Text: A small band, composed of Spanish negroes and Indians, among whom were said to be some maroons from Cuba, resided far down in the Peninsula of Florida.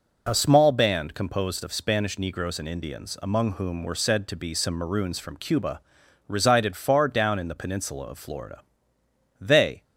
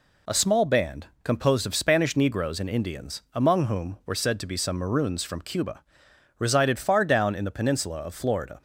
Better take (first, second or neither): second